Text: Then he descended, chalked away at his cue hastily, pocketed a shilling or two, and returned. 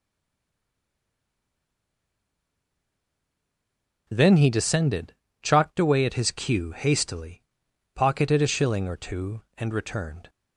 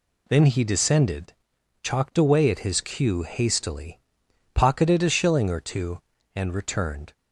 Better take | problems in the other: second | stays silent before the first word; strong; until 4.0 s; 4.0 s long

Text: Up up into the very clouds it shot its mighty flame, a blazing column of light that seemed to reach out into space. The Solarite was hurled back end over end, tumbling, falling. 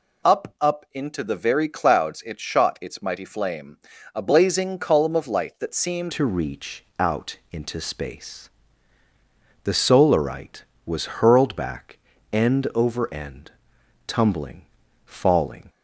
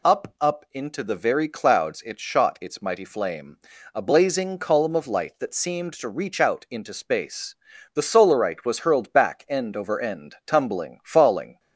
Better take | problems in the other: second | changes voice at "to"; from 6.1 s on; 9.5 s long // pauses between "reach" and "out"; slight; at 6.8 s; 0.16 s long // pauses between "back" and "end"; at 11.9 s; 0.38 s long

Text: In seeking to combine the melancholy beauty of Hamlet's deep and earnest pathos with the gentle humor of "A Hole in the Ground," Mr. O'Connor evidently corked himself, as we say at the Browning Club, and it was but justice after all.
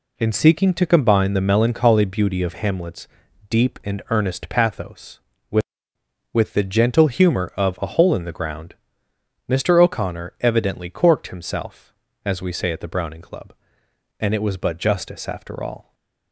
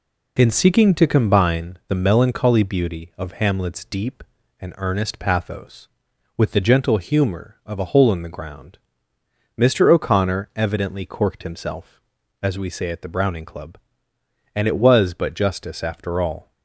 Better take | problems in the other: second | pauses between "Hamlet's" and "deep"; at 3.0 s; 0.44 s long // says "with" twice; at 6.3 s // stays silent after the last word; slight; from 15.8 s on; 0.5 s long

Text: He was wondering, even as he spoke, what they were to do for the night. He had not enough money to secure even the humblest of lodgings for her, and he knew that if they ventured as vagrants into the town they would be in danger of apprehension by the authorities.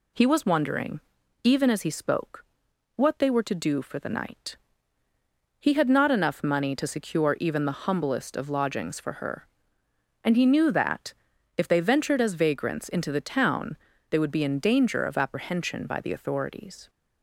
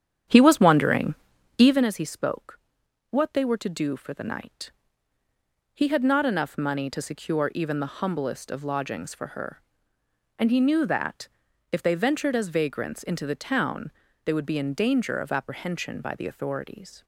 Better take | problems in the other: first | starts louder than the rest; strong; until 1.9 s; 9 dB // pauses between "that" and "if"; at 11.2 s; 0.44 s long; also in the first // pauses between "town" and "they"; slight; at 13.8 s; 0.34 s long; slight in the first

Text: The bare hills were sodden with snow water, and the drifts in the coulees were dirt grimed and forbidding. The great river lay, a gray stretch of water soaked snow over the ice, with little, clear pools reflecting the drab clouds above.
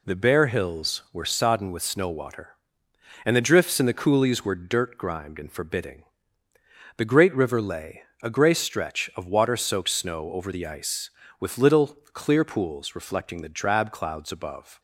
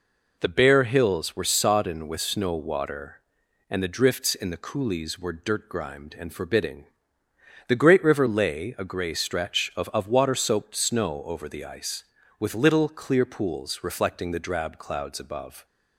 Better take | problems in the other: first | says "of" twice; at 9.9 s

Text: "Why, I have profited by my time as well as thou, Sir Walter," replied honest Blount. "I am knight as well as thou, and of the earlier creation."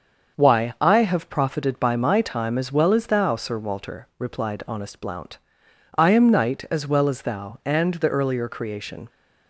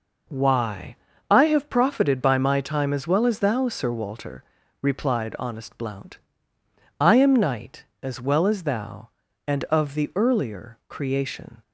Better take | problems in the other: second | starts louder than the rest; until 1.4 s; 6.5 dB // skips "of"; at 7.9 s

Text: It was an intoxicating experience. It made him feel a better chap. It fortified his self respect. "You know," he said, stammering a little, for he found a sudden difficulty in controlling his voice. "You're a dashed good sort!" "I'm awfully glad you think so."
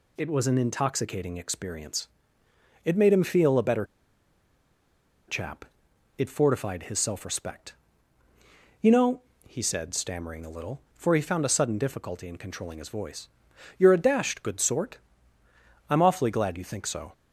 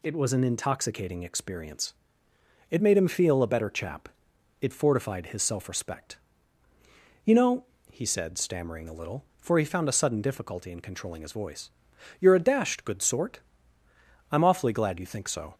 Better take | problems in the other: second | pauses between "better" and "chap"; strong; at 3.8 s; 1.4 s long

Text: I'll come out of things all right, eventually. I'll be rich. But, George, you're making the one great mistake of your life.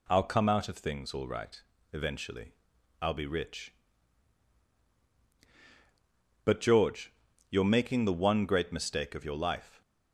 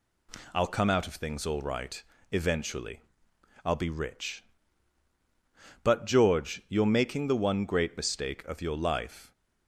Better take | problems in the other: neither | none

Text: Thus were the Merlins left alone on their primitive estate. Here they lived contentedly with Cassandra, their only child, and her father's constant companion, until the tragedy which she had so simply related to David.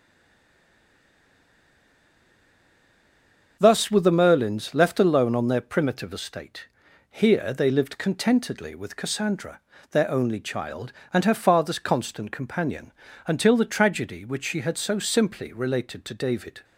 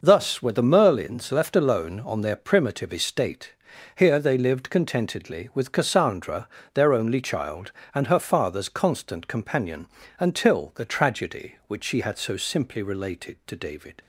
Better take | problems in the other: second | stays silent before the first word; strong; until 3.5 s; 3.5 s long // starts louder than the rest; until 4.6 s; 6.5 dB

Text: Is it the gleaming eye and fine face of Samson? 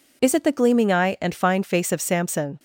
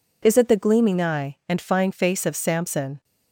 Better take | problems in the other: neither | none

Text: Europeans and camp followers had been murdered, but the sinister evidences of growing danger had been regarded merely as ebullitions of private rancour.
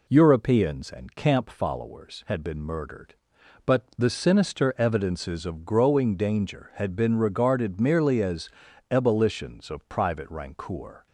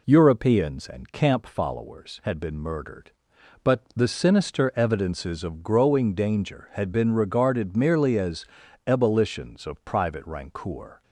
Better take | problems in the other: neither | pauses between "as" and "ebullitions"; the same in both

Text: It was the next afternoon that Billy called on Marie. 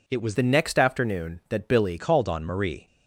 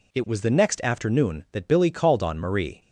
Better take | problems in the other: second | changes voice from "the" to "Billy"; from 0.3 to 1.9 s; 1.6 s long

